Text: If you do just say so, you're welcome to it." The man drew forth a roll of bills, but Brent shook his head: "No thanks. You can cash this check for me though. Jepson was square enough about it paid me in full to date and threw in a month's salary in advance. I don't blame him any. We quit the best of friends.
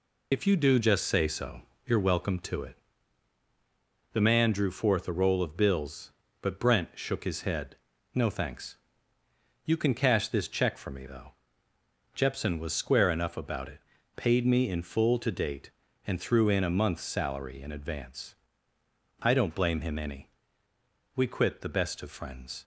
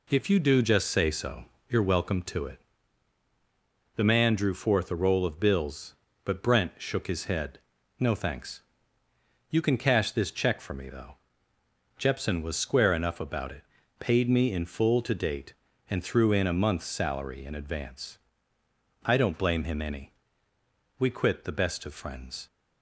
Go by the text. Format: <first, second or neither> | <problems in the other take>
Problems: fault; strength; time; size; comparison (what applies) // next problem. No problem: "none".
second | loses the start of "If"; at 0.3 s; 75 ms // pauses between "it" and "paid"; slight; at 13.8 s; 0.34 s long; slight in the second